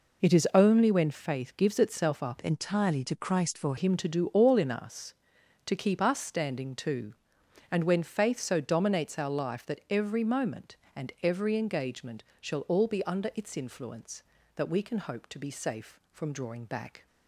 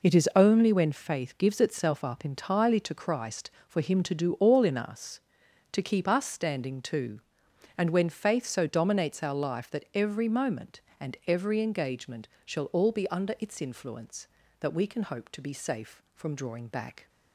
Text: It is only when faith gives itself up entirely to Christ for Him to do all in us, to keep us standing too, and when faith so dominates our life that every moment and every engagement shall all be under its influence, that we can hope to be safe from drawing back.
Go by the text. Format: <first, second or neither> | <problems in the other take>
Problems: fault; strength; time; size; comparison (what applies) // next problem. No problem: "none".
second | changes voice from "entirely" to "for"; from 2.4 to 3.7 s; 1.3 s long // pauses between "engagement" and "shall"; slight; at 12.2 s; 0.18 s long; slight in the second